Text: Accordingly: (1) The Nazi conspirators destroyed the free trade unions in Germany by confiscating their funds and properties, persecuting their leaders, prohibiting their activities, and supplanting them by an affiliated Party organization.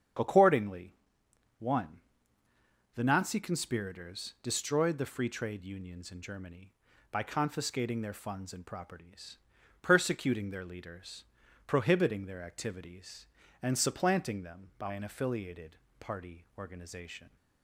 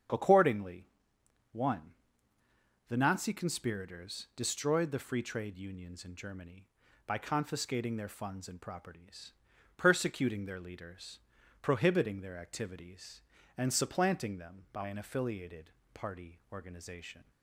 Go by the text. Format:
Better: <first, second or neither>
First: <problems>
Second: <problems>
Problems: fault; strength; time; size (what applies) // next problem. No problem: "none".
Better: neither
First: starts louder than the rest; strong; until 1.8 s; 8 dB // pauses between "affiliated" and "Party"; slight; at 15.7 s; 0.24 s long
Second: starts louder than the rest; strong; until 1.7 s; 8 dB // pauses between "affiliated" and "Party"; slight; at 15.6 s; 0.24 s long